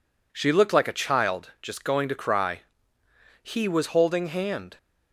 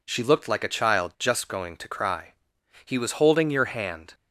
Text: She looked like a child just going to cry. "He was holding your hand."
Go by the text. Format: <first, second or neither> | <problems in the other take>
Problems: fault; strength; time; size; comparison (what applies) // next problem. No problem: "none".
second | skips "your"; at 4.2 s